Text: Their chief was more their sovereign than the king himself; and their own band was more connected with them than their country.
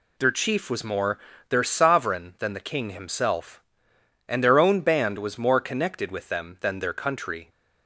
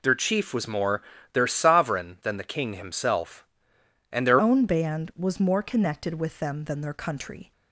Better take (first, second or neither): first